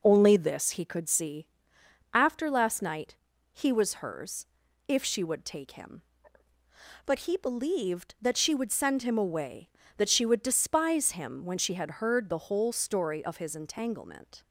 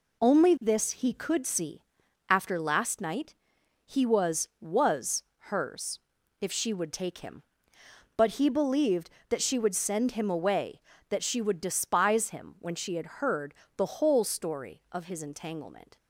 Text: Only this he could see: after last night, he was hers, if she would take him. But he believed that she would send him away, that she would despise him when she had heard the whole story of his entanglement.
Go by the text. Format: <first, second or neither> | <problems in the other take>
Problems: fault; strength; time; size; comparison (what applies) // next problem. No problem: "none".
first | says "was" twice; at 4.6 s // pauses between "heard" and "the"; slight; at 13.5 s; 0.24 s long